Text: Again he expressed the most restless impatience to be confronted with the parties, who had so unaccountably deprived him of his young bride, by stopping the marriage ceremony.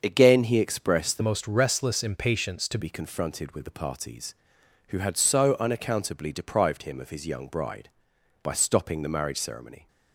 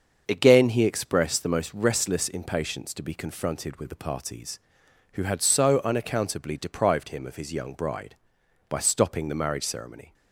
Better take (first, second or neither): second